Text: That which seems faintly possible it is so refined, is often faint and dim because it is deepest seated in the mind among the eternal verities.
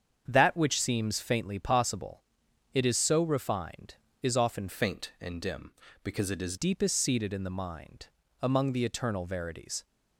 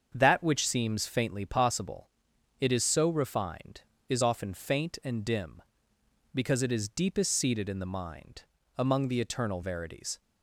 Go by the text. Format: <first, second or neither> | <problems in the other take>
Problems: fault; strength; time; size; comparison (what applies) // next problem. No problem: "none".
second | starts louder than the rest; strong; until 1.2 s; 7.5 dB; also in the second // pauses between "possible" and "it"; noticeable; at 2.2 s; 0.52 s long; noticeable in the second // changes voice from "faint" to "is"; from 4.6 to 6.5 s; 1.9 s long // pauses between "mind" and "among"; slight; at 8.0 s; 0.34 s long; slight in the second